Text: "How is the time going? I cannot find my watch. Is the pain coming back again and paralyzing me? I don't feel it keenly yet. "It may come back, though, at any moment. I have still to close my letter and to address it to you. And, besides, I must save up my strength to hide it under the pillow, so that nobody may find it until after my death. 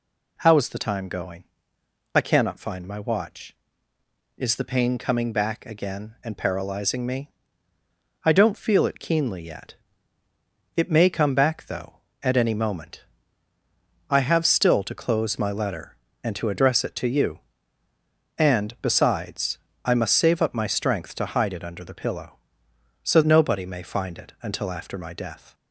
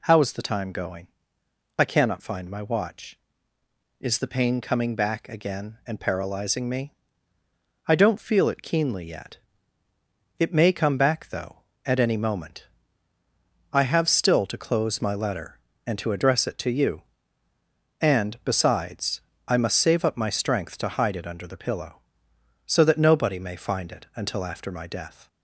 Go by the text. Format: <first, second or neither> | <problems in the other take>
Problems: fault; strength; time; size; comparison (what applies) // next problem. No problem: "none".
second | skips "that"; at 23.2 s